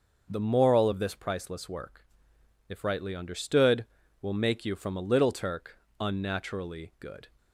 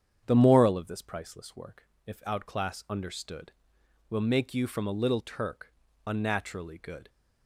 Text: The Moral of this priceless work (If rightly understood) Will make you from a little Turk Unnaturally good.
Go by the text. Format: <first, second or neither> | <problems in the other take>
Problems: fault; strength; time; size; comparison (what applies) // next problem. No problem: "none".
first | starts louder than the rest; strong; until 1.2 s; 8 dB; noticeable in the first // says "outclass" for "rightly"; at 2.2 s // pauses between "Turk" and "Unnaturally"; slight; at 5.7 s; 0.32 s long; slight in the first